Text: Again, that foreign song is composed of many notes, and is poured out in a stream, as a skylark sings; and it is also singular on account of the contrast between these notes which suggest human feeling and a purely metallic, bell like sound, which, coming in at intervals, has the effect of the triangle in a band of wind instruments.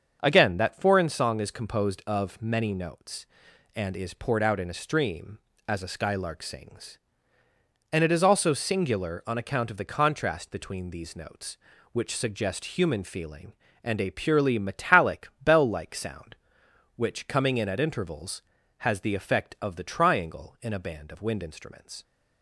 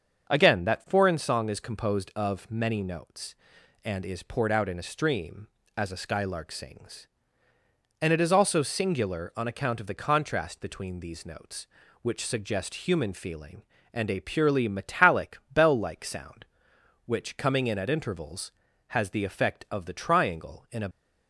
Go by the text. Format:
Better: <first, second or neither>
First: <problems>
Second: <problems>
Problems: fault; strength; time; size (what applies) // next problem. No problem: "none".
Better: first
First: starts louder than the rest; until 1.2 s; 7 dB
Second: starts louder than the rest; until 1.3 s; 7 dB // stops before "band of wind instruments"; at 20.9 s